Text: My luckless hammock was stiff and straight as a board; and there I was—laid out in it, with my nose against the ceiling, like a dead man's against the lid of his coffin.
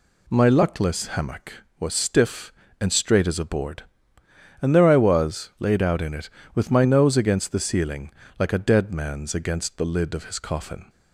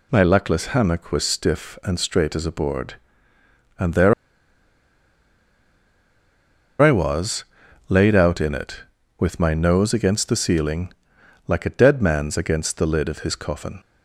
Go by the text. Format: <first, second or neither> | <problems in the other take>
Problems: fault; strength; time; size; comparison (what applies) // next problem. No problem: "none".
first | pauses between "there" and "I"; strong; at 4.1 s; 2.6 s long